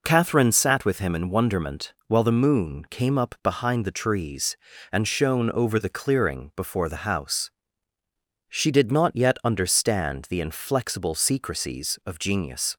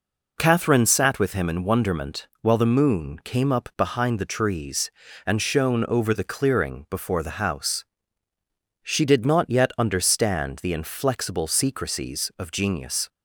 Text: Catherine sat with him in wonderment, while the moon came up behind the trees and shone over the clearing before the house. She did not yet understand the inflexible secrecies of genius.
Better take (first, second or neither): neither